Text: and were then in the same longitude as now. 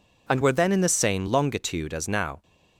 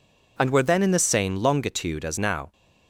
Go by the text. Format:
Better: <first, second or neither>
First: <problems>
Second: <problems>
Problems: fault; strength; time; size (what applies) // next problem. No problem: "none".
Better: neither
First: none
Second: none